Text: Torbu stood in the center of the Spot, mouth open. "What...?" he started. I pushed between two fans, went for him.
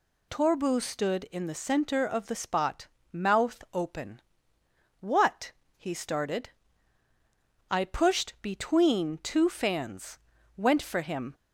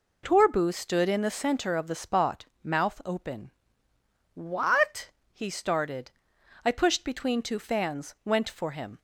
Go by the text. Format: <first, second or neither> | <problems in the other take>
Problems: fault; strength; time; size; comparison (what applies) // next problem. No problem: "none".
neither | none